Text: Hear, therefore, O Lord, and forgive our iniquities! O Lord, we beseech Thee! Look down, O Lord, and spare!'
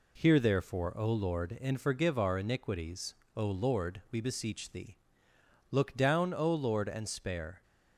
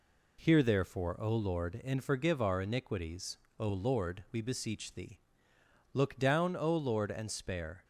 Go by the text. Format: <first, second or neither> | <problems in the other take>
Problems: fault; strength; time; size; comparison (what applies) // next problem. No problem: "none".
neither | none